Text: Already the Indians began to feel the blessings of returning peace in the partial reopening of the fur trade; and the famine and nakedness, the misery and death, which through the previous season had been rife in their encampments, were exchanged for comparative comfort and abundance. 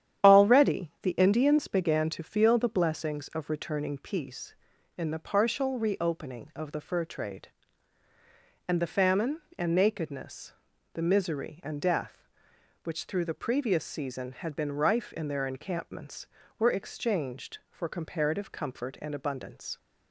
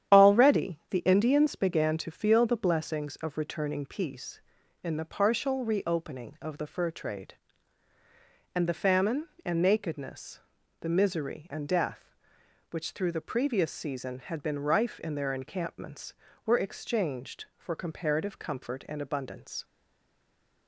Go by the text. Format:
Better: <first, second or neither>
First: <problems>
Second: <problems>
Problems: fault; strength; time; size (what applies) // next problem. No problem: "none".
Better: first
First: starts louder than the rest; strong; until 1.3 s; 10 dB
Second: starts louder than the rest; strong; until 1.2 s; 10 dB // stays silent after the last word; from 19.6 s on; 1.0 s long